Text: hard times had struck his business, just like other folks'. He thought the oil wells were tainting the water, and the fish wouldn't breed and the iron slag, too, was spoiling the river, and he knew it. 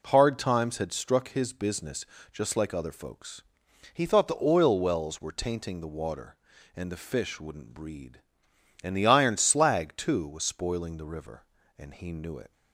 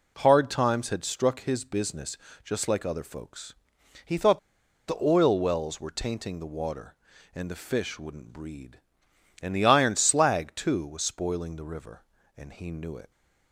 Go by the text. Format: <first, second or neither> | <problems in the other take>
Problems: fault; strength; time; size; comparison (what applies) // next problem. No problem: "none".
first | pauses between "thought" and "the"; noticeable; at 4.3 s; 0.49 s long